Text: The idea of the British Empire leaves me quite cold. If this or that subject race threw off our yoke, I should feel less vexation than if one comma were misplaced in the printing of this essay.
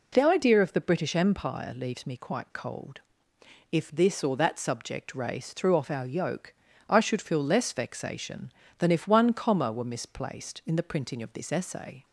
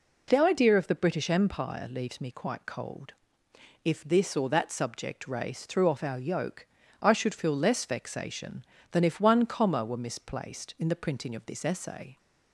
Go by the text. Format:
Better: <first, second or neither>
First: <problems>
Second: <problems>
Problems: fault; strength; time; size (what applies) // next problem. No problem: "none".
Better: neither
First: none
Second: none